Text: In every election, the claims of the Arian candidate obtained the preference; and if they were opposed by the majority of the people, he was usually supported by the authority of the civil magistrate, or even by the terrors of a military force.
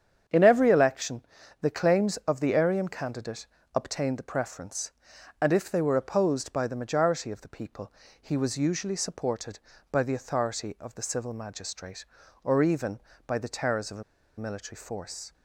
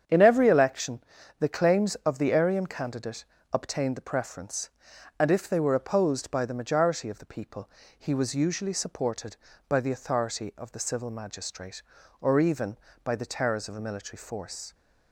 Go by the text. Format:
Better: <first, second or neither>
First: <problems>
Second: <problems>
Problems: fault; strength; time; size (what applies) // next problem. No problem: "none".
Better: second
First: starts louder than the rest; strong; until 1.6 s; 8 dB // pauses between "candidate" and "obtained"; slight; at 3.4 s; 0.26 s long // pauses between "a" and "military"; slight; at 14.0 s; 0.35 s long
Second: starts louder than the rest; strong; until 1.4 s; 8 dB // pauses between "candidate" and "obtained"; slight; at 3.2 s; 0.26 s long